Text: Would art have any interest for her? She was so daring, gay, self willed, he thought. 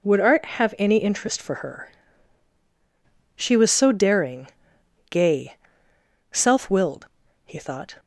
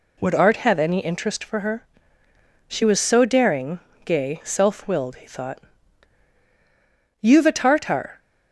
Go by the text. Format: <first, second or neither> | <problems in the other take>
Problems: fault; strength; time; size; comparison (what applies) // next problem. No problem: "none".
first | goes on to say "You've a Tartar"; noticeable; from 7.2 s on; 0.98 s long